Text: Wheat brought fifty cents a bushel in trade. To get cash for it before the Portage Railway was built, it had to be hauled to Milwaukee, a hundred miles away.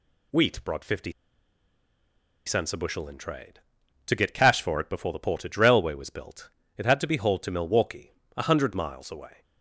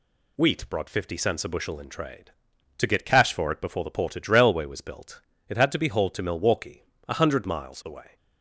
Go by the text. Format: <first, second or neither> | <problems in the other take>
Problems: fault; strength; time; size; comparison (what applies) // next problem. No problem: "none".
second | pauses between "fifty" and "cents"; strong; at 1.1 s; 1.3 s long